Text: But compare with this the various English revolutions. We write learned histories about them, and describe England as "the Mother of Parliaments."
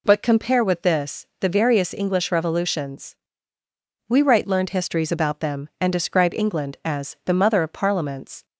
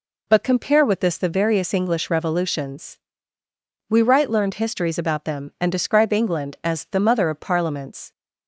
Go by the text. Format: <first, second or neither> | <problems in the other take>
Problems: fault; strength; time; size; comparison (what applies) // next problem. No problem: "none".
neither | none